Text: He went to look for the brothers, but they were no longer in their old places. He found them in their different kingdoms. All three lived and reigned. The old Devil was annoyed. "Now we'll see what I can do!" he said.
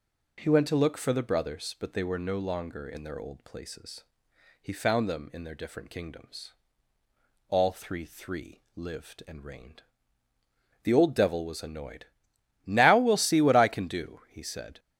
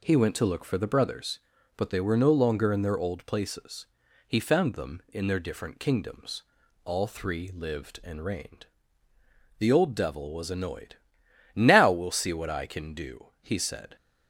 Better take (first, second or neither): second